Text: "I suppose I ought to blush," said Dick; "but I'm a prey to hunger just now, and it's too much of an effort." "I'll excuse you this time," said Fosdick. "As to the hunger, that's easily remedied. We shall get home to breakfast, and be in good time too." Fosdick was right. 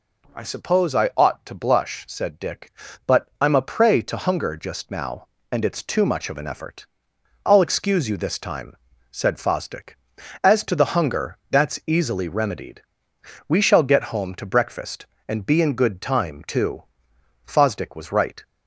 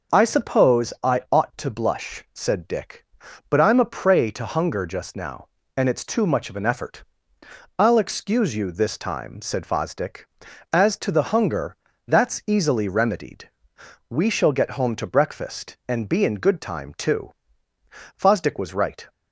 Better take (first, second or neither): neither